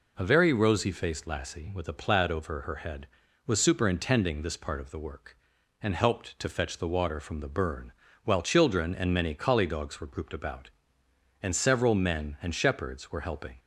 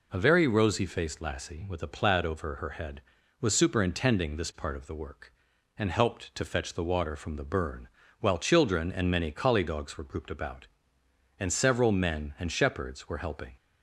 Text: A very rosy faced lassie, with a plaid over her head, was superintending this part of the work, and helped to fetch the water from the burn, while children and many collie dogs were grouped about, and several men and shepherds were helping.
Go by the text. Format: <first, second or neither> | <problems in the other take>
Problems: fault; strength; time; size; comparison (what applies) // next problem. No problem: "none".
neither | none